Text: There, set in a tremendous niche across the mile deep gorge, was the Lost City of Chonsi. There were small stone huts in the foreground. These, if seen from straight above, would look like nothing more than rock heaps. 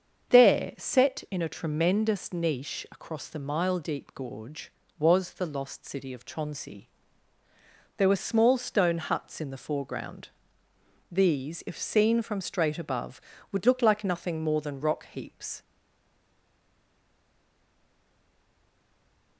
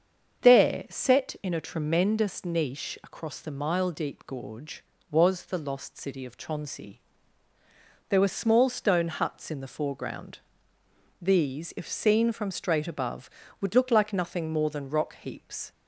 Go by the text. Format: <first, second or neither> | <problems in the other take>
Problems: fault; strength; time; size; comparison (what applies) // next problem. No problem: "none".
second | starts louder than the rest; until 1.4 s; 7 dB; also in the second // stays silent after the last word; strong; from 15.6 s on; 3.7 s long